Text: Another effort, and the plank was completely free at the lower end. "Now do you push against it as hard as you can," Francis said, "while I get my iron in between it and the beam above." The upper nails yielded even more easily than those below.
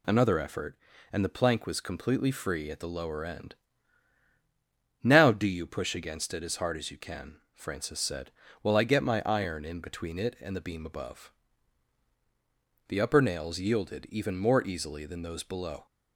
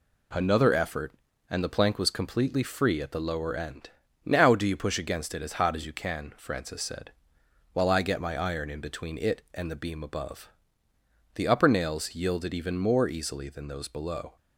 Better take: first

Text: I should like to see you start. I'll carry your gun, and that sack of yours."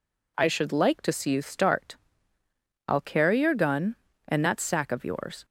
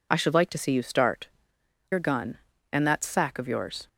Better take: first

